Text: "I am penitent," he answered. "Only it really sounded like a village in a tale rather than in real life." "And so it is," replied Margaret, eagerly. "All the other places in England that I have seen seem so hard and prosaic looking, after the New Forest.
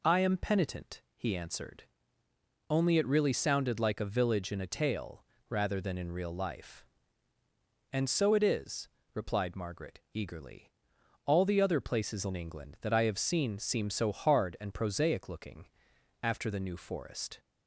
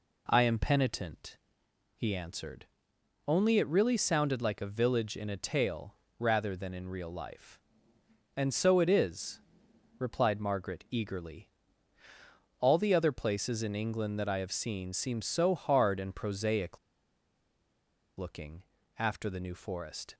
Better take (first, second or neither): first